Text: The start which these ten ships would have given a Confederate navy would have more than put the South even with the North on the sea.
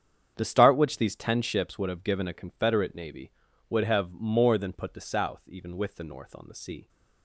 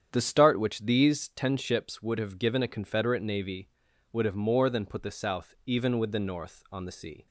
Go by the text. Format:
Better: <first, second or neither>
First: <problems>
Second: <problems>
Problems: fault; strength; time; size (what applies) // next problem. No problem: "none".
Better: neither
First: starts louder than the rest; strong; until 1.3 s; 8 dB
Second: starts louder than the rest; strong; until 1.1 s; 8.5 dB